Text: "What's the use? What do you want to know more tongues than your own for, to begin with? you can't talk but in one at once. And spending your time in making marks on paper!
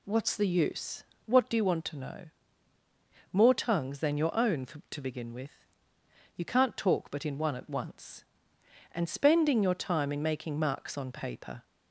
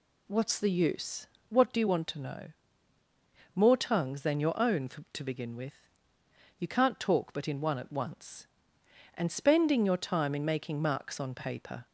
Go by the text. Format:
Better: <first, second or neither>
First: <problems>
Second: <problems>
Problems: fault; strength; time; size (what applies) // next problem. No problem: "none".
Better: neither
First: pauses between "know" and "more"; at 2.2 s; 1.0 s long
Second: pauses between "know" and "more"; at 2.5 s; 1.0 s long